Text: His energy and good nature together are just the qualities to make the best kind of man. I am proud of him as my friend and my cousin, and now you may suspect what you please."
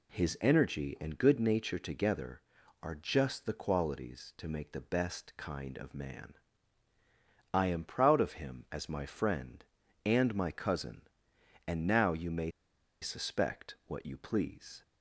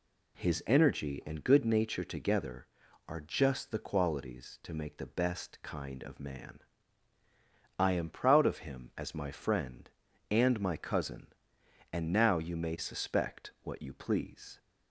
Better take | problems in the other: second | pauses between "may" and "suspect"; noticeable; at 12.5 s; 0.51 s long

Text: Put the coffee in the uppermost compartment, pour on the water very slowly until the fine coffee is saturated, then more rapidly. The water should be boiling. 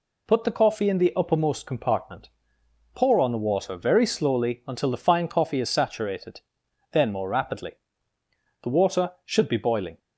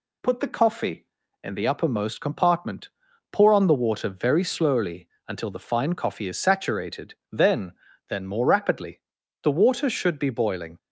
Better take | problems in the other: first | pauses between "slowly" and "until"; slight; at 5.0 s; 0.20 s long // says "then" twice; at 8.0 s

